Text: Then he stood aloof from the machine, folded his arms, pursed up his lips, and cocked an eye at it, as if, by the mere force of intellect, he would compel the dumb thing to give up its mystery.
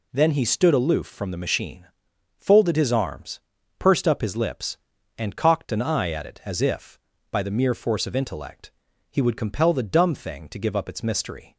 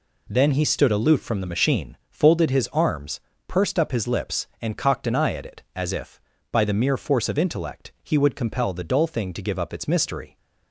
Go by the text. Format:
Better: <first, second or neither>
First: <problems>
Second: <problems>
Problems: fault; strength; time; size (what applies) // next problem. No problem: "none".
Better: first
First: none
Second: says "dull" for "dumb"; at 8.8 s